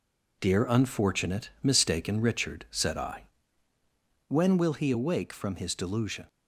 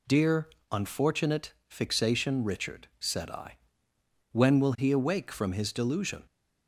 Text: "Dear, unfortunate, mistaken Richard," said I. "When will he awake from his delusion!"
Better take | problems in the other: first | says "fixation" for "mistaken"; at 1.6 s

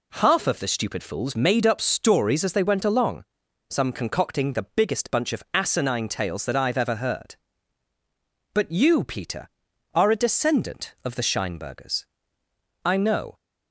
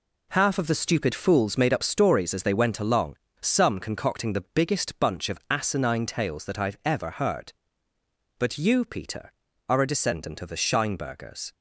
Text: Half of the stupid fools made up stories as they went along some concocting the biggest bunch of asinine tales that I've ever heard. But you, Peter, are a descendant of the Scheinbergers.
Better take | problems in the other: second | pauses between "along" and "some"; noticeable; at 3.2 s; 0.48 s long; slight in the second // goes on to say "I know"; from 12.8 s on; 0.52 s long

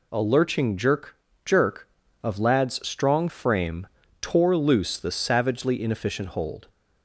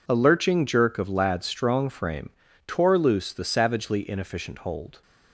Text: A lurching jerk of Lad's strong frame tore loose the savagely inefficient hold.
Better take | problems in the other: second | says "jerk" twice; at 1.4 s // pauses between "frame" and "tore"; slight; at 3.8 s; 0.34 s long; also in the second

